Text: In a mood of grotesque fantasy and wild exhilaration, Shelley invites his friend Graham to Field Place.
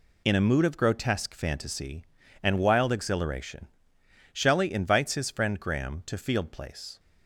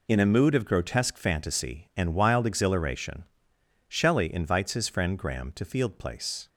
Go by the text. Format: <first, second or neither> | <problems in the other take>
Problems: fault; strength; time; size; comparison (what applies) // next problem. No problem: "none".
neither | none